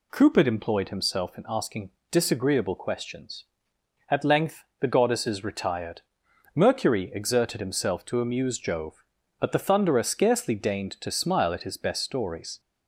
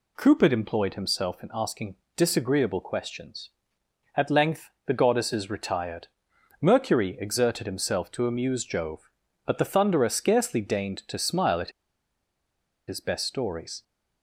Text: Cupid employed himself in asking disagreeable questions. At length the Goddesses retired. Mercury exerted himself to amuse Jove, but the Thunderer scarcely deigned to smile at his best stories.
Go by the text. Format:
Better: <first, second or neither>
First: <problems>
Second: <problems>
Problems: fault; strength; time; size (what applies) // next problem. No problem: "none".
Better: first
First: pauses between "asking" and "disagreeable"; slight; at 1.8 s; 0.20 s long // pauses between "length" and "the"; slight; at 4.6 s; 0.16 s long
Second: pauses between "asking" and "disagreeable"; slight; at 1.9 s; 0.20 s long // pauses between "length" and "the"; slight; at 4.6 s; 0.16 s long // pauses between "at" and "his"; at 11.7 s; 1.1 s long